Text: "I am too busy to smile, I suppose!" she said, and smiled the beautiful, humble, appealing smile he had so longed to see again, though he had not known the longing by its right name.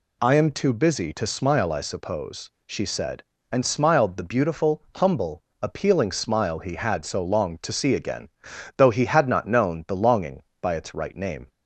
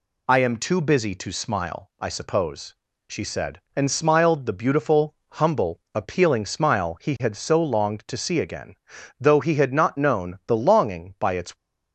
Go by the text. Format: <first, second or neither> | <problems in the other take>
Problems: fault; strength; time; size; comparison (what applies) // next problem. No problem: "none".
first | stops before "right name"; at 11.5 s